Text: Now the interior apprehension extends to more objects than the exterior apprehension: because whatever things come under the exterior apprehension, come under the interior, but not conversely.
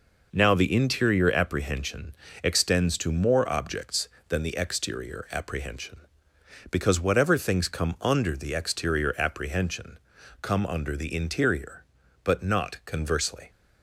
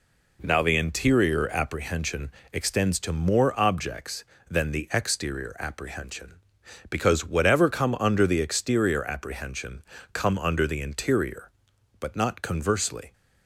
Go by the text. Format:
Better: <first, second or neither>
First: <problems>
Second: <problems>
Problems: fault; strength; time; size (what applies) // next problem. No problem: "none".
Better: first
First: pauses between "apprehension" and "extends"; slight; at 2.1 s; 0.30 s long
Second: pauses between "apprehension" and "extends"; slight; at 2.3 s; 0.22 s long // skips "things"; at 7.6 s